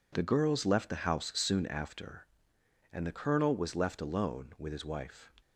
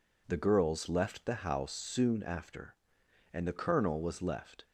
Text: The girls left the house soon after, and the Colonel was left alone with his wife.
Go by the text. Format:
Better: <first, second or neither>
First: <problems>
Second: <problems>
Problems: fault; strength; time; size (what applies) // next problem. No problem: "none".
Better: first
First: none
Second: stops before "alone with his wife"; at 4.6 s